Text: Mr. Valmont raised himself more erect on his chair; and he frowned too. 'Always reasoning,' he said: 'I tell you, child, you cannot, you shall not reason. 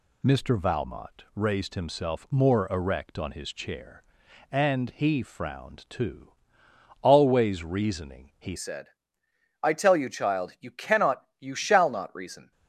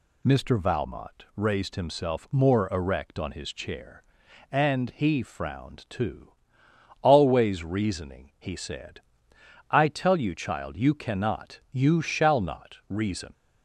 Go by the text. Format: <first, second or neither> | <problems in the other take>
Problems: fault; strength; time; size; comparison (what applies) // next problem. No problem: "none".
second | changes voice at "said"; from 8.5 s on; 4.0 s long